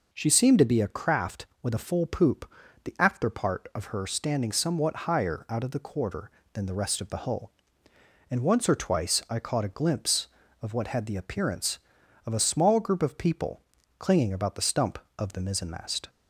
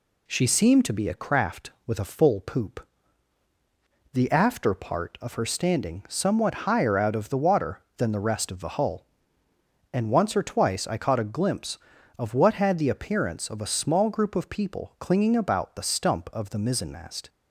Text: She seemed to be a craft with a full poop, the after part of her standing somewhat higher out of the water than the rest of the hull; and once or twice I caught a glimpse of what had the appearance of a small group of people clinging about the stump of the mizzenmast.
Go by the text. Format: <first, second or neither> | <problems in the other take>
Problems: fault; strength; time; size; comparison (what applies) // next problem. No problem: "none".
second | says "quarter" for "water"; at 5.7 s // pauses between "people" and "clinging"; at 13.6 s; 0.38 s long